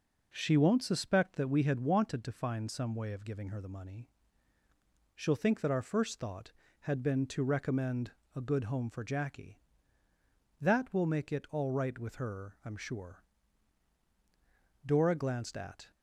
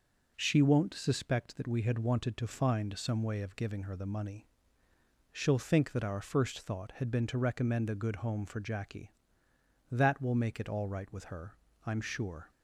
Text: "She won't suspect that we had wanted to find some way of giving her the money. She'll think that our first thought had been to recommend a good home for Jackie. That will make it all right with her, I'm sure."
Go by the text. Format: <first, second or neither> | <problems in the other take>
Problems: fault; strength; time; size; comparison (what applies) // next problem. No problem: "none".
second | pauses between "recommend" and "a"; slight; at 8.1 s; 0.22 s long // goes on to say "Dora glanced at"; noticeable; from 14.8 s on; 1.0 s long